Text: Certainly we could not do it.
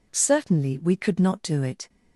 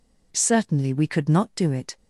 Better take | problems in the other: neither | none

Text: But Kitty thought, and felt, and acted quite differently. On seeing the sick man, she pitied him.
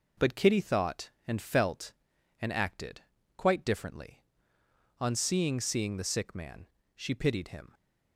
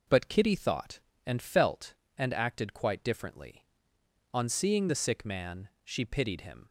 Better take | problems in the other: second | pauses between "acted" and "quite"; slight; at 3.0 s; 0.34 s long // says "seeing" twice; at 5.5 s

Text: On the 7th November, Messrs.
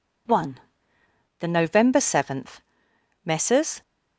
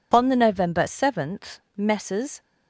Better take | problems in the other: second | says "One" for "On"; at 0.2 s

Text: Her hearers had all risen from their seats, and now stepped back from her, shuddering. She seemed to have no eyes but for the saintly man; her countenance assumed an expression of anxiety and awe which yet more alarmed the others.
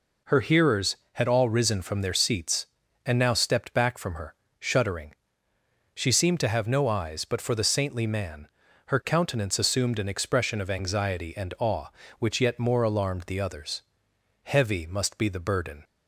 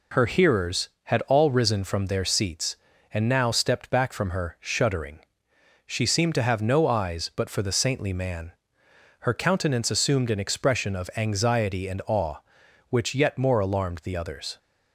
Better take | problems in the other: second | goes on to say "Heavy must be the burden"; from 14.4 s on; 1.4 s long

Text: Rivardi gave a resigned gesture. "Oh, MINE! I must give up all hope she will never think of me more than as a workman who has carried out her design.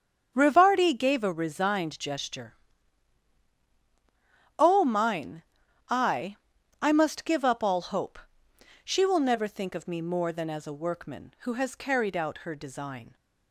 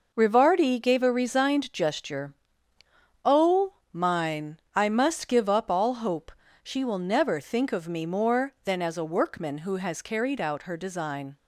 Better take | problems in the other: second | starts louder than the rest; until 1.3 s; 7 dB // says "I" twice; at 6.8 s // pauses between "hope" and "she"; noticeable; at 8.1 s; 0.66 s long; slight in the second

